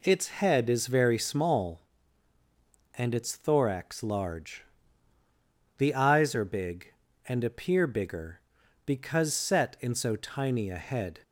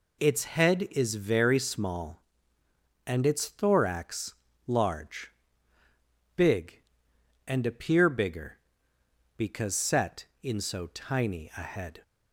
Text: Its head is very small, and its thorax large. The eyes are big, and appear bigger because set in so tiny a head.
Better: first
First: none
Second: pauses between "thorax" and "large"; slight; at 4.3 s; 0.32 s long // skips "The eyes are"; at 5.8 s

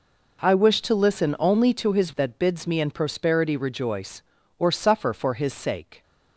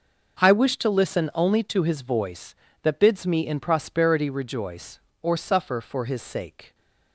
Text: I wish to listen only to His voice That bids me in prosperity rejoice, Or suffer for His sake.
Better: second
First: skips "voice"; at 2.1 s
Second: none

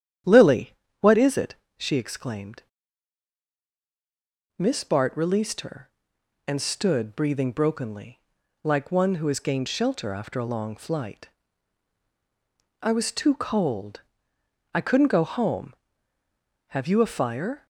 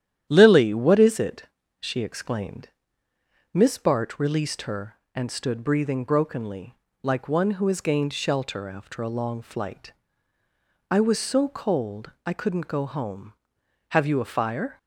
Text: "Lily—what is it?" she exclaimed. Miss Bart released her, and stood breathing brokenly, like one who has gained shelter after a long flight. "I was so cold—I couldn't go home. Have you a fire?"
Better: second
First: starts louder than the rest; strong; until 1.8 s; 9.5 dB // says "too" for "so"; at 13.1 s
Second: starts louder than the rest; strong; until 1.3 s; 11 dB

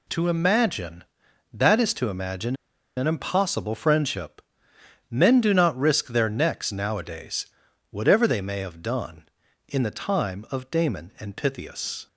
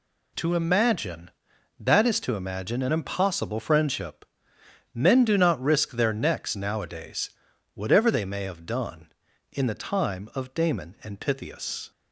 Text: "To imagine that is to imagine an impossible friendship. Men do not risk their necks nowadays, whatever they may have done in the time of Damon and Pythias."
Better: second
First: pauses between "imagine" and "an"; at 2.5 s; 0.40 s long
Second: none

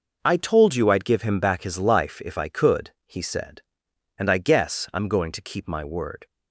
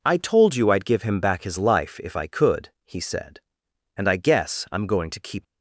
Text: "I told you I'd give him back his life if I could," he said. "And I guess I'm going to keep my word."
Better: first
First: none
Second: stops before "my word"; at 5.4 s

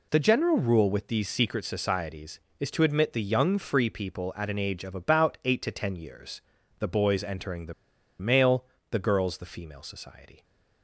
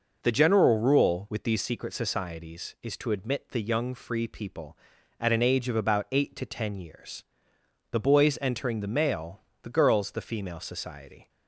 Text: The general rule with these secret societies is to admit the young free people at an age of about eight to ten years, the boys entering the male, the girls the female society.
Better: second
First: pauses between "the" and "male"; noticeable; at 7.7 s; 0.47 s long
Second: none

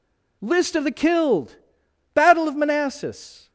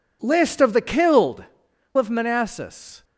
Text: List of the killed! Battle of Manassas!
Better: first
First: none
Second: skips "Battle"; at 1.7 s

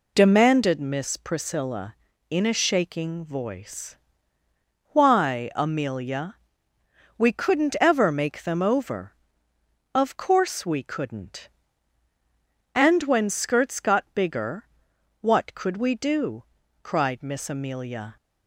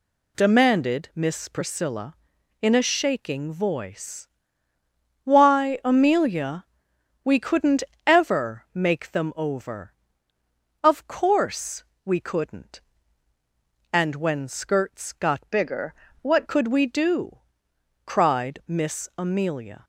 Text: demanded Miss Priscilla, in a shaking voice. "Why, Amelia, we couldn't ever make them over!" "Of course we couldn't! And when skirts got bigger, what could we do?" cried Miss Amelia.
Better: first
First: none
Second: pauses between "couldn't" and "ever"; slight; at 7.8 s; 0.24 s long // pauses between "course" and "we"; slight; at 11.8 s; 0.20 s long // changes voice from "bigger" to "what"; from 15.5 to 16.4 s; 0.9 s long

